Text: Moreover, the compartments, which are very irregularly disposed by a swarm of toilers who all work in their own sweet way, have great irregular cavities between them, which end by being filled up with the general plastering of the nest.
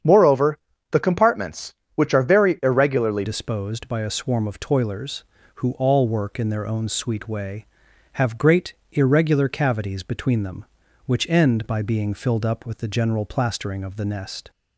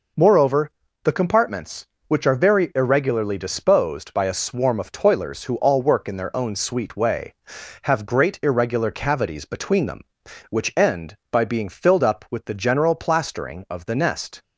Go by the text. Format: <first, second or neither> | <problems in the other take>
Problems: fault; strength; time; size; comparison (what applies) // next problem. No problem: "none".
second | starts louder than the rest; strong; until 1.3 s; 8 dB // changes voice at "disposed"; from 3.2 s on; 11.2 s long // pauses between "great" and "irregular"; slight; at 8.7 s; 0.18 s long